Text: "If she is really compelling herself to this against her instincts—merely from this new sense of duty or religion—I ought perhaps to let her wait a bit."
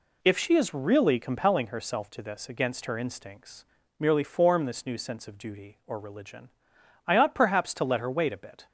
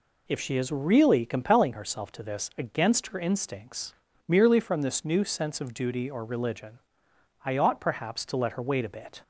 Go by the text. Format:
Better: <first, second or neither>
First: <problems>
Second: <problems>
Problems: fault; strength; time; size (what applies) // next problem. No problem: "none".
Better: second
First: says "form" for "from"; at 4.2 s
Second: none